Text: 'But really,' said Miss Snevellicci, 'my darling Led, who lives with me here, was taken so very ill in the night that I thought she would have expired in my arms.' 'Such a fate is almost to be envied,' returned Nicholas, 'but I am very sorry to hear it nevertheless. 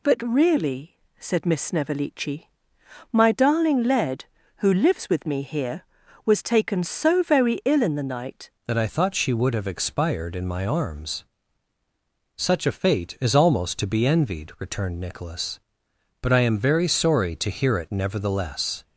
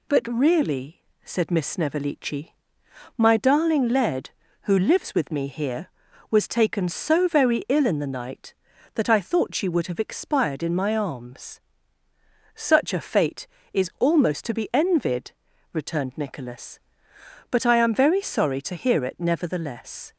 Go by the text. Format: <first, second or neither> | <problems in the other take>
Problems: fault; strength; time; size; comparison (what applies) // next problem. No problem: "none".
second | changes voice at "that"; from 8.6 s on; 10.2 s long